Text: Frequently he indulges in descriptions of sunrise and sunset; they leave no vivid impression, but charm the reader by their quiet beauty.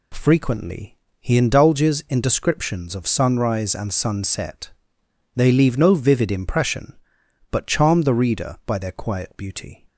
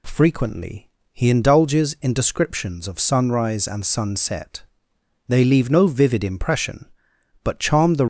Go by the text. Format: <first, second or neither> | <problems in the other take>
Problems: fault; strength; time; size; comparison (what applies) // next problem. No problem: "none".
first | pauses between "Frequently" and "he"; slight; at 0.8 s; 0.22 s long; slight in the first // stops before "reader by their quiet beauty"; at 8.0 s